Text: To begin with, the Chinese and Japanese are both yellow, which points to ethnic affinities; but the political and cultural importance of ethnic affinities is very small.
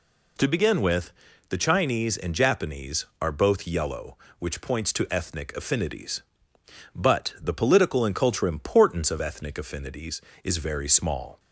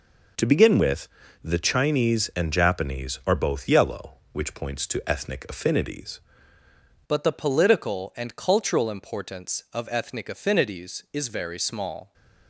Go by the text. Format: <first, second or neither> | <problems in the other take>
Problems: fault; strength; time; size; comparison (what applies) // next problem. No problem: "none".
first | changes voice at "but"; from 7.0 s on; 5.1 s long